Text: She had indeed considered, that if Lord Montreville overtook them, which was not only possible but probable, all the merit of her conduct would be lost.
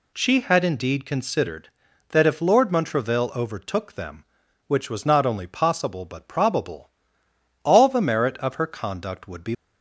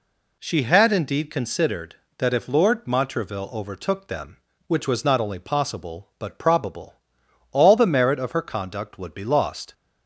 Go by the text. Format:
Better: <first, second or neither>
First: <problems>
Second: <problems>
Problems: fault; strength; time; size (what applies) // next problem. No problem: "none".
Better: second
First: stops before "lost"; at 9.5 s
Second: none